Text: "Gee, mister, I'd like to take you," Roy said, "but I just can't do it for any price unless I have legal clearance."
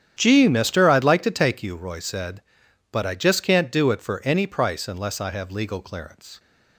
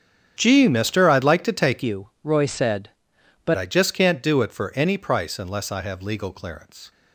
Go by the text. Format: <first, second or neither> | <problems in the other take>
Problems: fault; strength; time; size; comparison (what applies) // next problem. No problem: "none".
first | starts louder than the rest; strong; until 1.3 s; 9.5 dB; strong in the first // changes voice from "you" to "but"; from 1.8 to 3.5 s; 1.7 s long